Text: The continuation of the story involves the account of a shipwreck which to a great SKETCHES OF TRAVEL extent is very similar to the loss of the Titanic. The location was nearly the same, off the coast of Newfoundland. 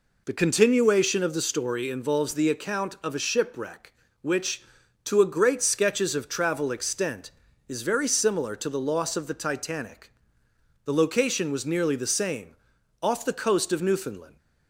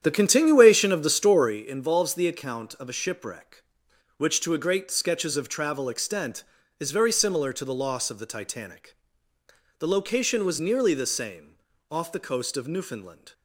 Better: first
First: none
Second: starts louder than the rest; strong; until 1.6 s; 9.5 dB

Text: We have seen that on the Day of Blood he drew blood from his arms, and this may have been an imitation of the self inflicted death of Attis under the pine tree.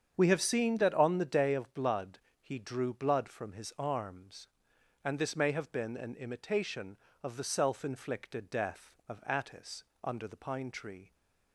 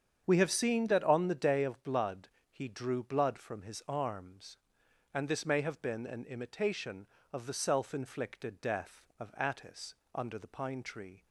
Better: neither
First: starts louder than the rest; strong; until 1.1 s; 7.5 dB // pauses between "Blood" and "he"; slight; at 2.2 s; 0.20 s long // pauses between "Attis" and "under"; slight; at 9.8 s; 0.22 s long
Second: starts louder than the rest; strong; until 1.2 s; 7.5 dB // pauses between "Blood" and "he"; slight; at 2.2 s; 0.20 s long // pauses between "Attis" and "under"; slight; at 9.9 s; 0.22 s long

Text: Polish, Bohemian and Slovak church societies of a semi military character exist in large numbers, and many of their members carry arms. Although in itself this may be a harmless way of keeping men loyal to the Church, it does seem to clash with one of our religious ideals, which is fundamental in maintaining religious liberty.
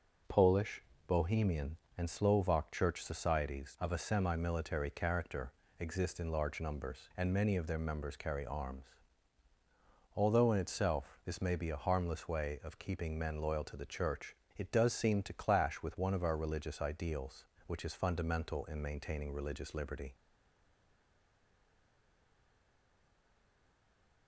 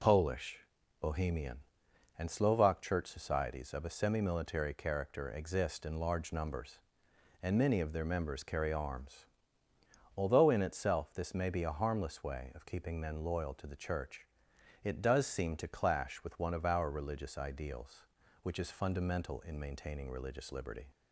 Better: second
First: pauses between "character" and "exist"; slight; at 5.5 s; 0.26 s long // stays silent after the last word; strong; from 20.1 s on; 4.1 s long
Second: none

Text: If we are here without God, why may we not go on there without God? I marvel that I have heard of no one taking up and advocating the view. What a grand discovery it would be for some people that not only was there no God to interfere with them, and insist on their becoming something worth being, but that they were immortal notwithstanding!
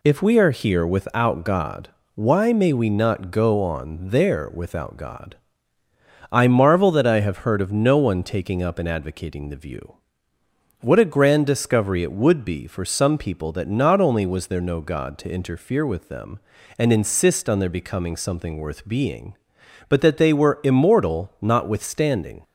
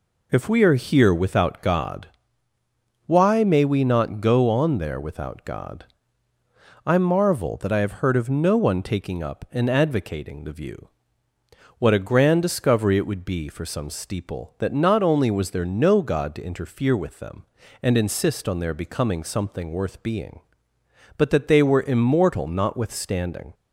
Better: first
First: none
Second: says "steeple" for "people"; at 13.8 s

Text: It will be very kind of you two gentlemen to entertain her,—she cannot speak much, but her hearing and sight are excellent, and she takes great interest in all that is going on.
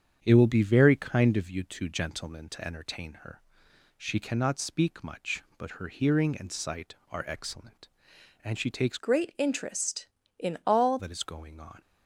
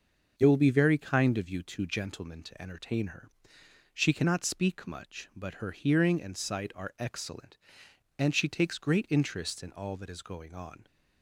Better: second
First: starts louder than the rest; strong; until 1.2 s; 8 dB // changes voice from "great" to "all"; from 8.9 to 10.9 s; 2.0 s long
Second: starts louder than the rest; noticeable; until 1.4 s; 6 dB

